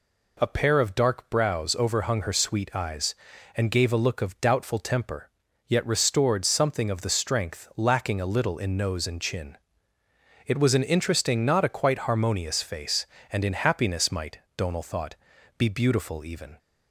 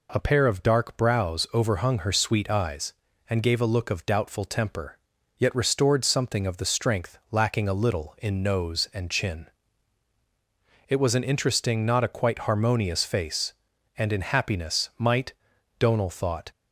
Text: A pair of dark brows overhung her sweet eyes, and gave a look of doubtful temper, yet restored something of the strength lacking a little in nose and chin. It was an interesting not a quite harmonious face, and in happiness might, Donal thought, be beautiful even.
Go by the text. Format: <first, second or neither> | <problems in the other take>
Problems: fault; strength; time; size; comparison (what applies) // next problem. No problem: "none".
first | stops before "be beautiful even"; at 16.5 s